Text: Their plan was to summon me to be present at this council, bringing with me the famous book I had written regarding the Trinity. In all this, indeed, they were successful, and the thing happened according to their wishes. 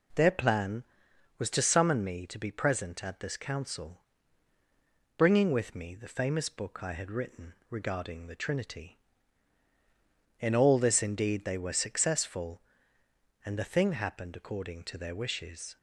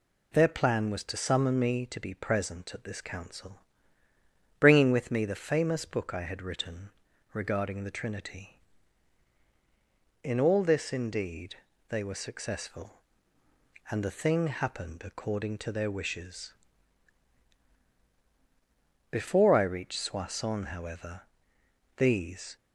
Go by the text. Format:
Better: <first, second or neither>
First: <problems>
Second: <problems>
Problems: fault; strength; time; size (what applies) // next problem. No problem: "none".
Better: first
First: pauses between "written" and "regarding"; slight; at 7.5 s; 0.16 s long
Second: pauses between "written" and "regarding"; at 6.8 s; 0.44 s long // goes on to say "Before I reached Soissons however these"; strong; from 19.0 s on; 3.4 s long